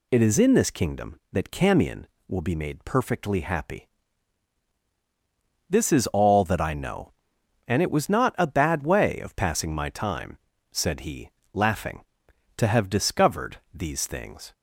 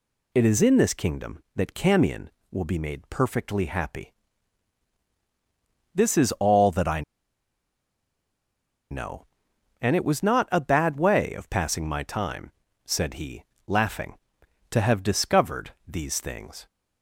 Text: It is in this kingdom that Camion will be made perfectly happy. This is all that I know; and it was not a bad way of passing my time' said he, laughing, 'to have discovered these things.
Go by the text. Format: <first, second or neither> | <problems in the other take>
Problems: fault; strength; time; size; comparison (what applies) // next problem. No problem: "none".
first | pauses between "I" and "know"; strong; at 7.0 s; 1.8 s long // pauses between "time" and "said"; slight; at 12.5 s; 0.34 s long; slight in the first